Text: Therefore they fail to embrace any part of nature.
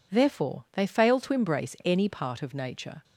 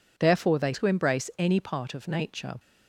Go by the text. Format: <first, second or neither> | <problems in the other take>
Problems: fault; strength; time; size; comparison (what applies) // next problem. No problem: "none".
first | skips "fail"; at 0.7 s